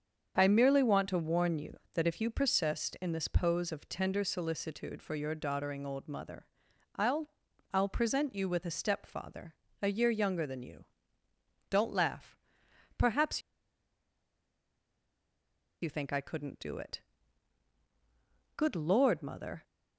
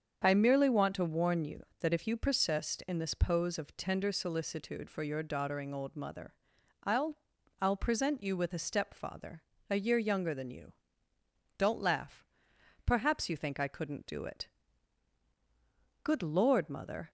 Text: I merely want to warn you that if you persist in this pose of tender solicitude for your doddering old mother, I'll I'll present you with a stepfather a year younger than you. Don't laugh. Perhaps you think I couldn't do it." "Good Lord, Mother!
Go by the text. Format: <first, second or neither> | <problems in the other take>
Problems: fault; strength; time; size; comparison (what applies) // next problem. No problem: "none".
second | starts louder than the rest; strong; until 1.3 s; 7 dB; strong in the second // pauses between "I'll" and "I'll"; at 7.2 s; 0.44 s long; also in the second // pauses between "stepfather" and "a"; slight; at 9.5 s; 0.26 s long; slight in the second // pauses between "Perhaps" and "you"; strong; at 13.4 s; 2.4 s long